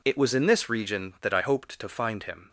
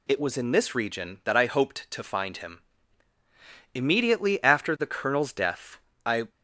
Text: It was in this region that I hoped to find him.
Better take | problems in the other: first | goes on to say "Immediately after the Colonel's death I"; strong; from 3.7 s on; 2.5 s long

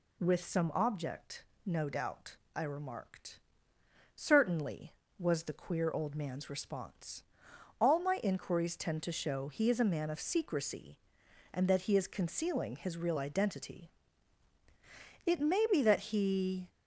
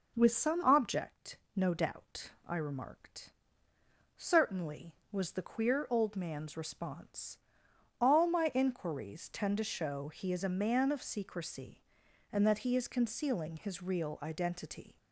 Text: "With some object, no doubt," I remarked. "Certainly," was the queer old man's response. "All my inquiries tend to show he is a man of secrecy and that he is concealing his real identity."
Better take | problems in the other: second | goes on to say "It may be that he"; from 15.2 s on; 1.4 s long

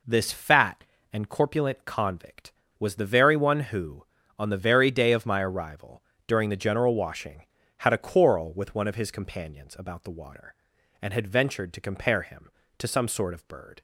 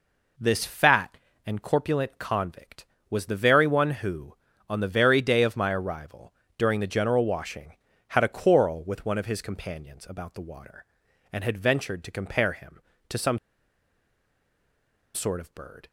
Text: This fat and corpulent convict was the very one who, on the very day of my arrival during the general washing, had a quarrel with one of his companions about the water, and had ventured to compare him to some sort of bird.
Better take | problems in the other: first | pauses between "arrival" and "during"; slight; at 6.3 s; 0.24 s long; slight in the first // pauses between "some" and "sort"; strong; at 13.3 s; 1.7 s long

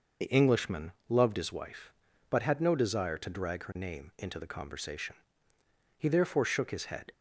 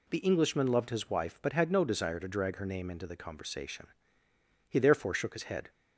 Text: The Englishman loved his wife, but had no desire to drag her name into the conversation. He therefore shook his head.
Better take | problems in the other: second | loses the start of "The"; at 0.2 s; 30 ms // pauses between "Englishman" and "loved"; slight; at 0.9 s; 0.18 s long

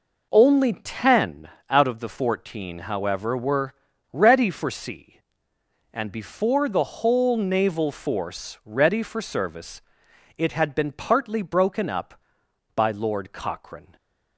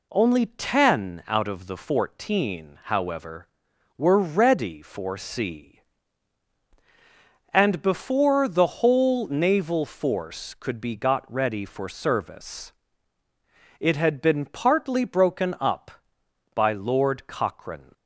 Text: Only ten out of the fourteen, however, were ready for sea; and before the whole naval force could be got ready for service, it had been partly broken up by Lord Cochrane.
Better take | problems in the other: second | pauses between "ten" and "out"; slight; at 1.4 s; 0.22 s long // pauses between "were" and "ready"; at 3.7 s; 0.41 s long // skips "could be got"; at 8.6 s

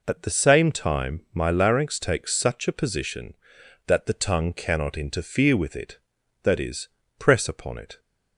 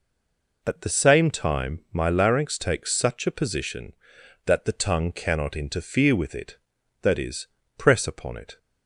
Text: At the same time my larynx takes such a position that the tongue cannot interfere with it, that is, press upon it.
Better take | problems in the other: first | stays silent before the first word; slight; until 0.6 s; 0.6 s long

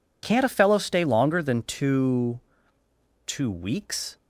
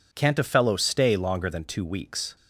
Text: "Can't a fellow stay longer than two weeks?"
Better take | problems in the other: second | says "two" twice; at 3.2 s

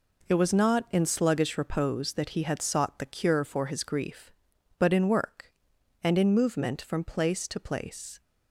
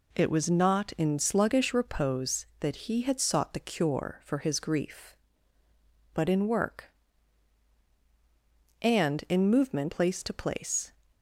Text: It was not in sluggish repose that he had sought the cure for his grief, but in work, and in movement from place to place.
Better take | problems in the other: first | skips "from"; at 9.9 s

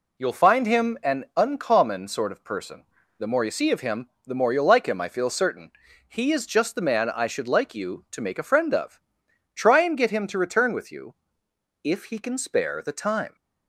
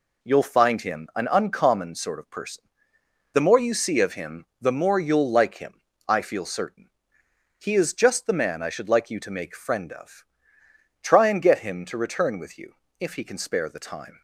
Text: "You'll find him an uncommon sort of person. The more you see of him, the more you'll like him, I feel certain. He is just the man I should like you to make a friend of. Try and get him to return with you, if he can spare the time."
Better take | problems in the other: first | skips "a"; at 9.5 s

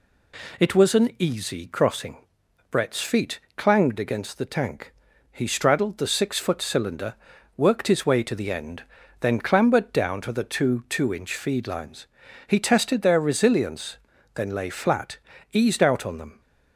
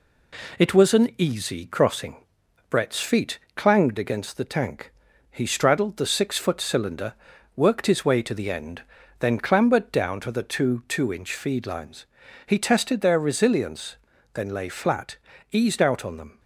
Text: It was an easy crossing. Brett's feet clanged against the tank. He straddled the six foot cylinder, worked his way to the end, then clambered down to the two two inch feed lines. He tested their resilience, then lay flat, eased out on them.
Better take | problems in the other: first | gets quieter; slight; throughout; 3 dB // pauses between "feet" and "clanged"; slight; at 3.3 s; 0.18 s long; slight in the first

